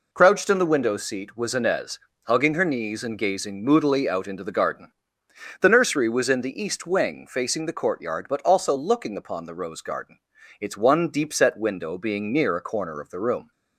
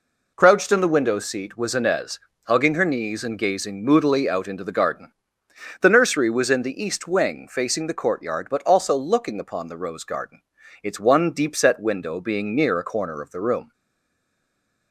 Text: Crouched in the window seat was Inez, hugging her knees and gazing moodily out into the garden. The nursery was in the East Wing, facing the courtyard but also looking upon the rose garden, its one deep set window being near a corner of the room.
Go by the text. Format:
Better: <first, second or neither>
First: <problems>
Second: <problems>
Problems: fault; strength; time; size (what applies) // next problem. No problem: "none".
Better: first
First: none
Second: stays silent after the last word; noticeable; from 13.7 s on; 1.2 s long